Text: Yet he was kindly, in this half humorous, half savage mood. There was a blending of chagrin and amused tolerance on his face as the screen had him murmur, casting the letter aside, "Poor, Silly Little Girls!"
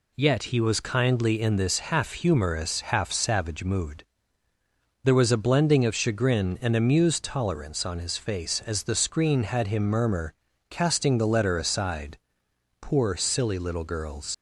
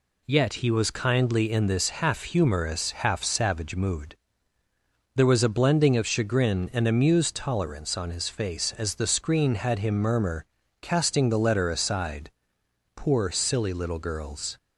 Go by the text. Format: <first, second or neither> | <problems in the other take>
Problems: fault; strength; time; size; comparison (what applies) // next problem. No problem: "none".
second | leaves "Girls" unfinished; at 14.3 s; 75 ms